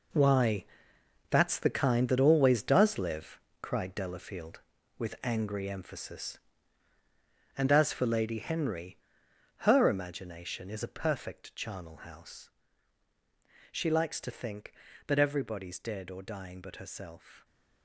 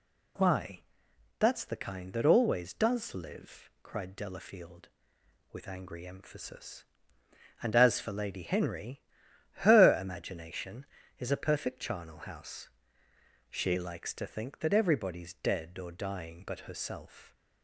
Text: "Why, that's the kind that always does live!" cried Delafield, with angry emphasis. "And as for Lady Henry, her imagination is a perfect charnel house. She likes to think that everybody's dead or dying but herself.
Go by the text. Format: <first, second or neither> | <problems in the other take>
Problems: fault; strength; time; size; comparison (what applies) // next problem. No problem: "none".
second | gets quieter; strong; throughout; 11.5 dB